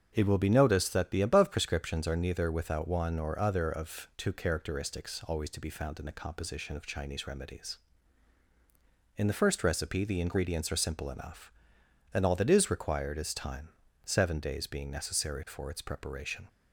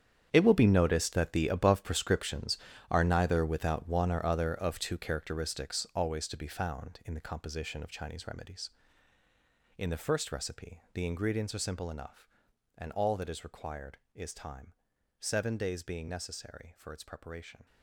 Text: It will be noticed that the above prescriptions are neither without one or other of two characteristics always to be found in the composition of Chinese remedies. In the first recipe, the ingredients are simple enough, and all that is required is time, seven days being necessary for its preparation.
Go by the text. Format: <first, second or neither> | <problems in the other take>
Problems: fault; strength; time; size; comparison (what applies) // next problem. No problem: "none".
first | gets quieter; strong; throughout; 14.5 dB // starts louder than the rest; strong; until 1.3 s; 8.5 dB; strong in the first